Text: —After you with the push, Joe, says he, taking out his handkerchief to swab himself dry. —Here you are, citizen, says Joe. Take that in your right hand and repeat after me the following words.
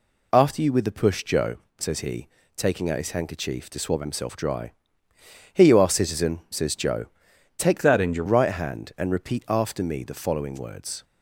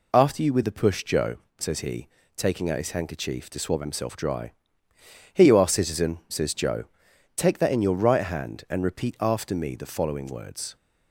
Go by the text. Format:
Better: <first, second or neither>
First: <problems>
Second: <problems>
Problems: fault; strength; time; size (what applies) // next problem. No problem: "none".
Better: second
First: changes voice from "that" to "your"; from 7.8 to 8.2 s; 0.4 s long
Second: none